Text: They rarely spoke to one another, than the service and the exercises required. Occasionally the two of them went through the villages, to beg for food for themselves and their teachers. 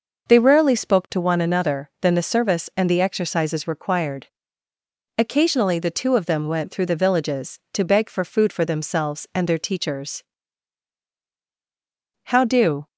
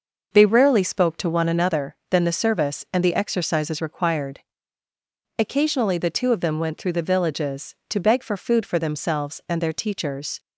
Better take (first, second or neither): second